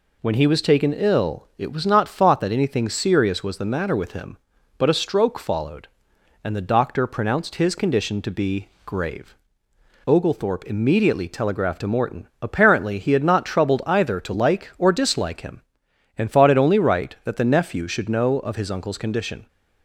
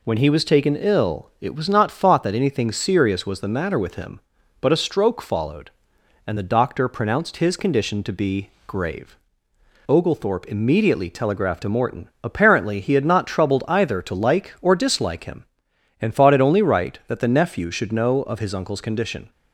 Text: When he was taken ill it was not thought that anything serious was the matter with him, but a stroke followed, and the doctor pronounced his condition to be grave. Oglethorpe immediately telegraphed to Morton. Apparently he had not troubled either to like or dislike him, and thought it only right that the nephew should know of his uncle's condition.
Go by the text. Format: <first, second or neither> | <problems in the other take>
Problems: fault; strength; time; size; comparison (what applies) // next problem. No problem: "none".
neither | pauses between "be" and "grave"; slight; the same in both